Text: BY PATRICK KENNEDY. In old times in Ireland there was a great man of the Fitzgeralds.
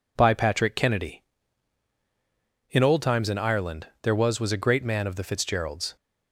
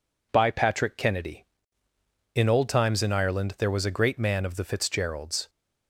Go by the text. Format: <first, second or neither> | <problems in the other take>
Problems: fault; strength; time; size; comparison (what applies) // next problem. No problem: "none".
second | pauses between "Ireland" and "there"; slight; at 3.8 s; 0.16 s long // says "was" twice; at 4.3 s